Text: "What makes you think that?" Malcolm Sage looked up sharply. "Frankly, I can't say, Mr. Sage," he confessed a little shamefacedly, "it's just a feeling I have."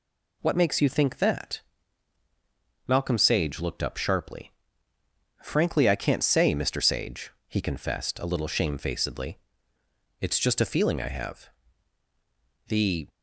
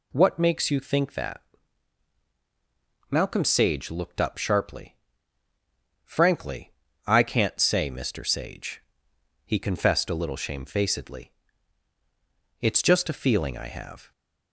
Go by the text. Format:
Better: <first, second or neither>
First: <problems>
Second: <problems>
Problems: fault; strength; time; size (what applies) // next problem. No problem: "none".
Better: second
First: goes on to say "The"; slight; from 12.6 s on; 0.42 s long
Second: none